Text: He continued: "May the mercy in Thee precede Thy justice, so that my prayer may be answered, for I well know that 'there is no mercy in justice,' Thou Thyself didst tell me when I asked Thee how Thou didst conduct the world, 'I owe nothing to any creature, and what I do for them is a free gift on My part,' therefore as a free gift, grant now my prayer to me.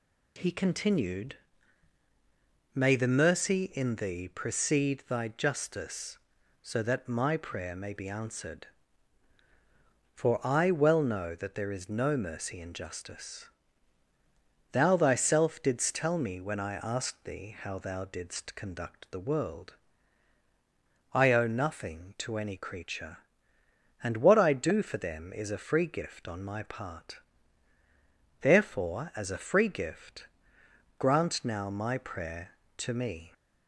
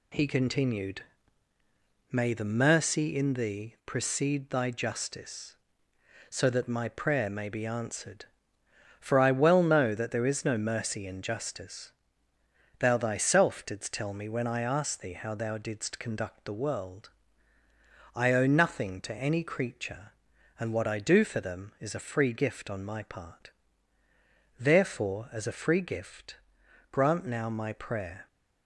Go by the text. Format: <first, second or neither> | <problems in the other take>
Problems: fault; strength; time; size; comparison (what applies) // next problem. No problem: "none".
first | stops before "to me"; at 28.2 s